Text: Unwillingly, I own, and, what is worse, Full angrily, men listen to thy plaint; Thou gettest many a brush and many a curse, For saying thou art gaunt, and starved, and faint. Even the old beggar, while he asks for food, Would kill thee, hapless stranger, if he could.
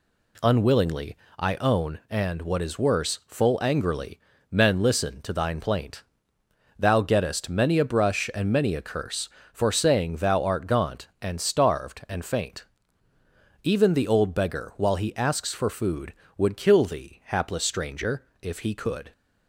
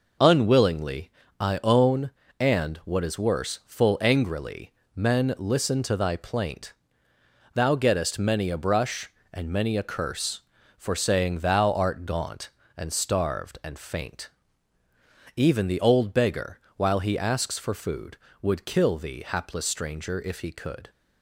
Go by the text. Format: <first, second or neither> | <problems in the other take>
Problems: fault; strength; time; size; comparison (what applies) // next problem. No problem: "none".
second | says "thine" for "thy"; at 5.3 s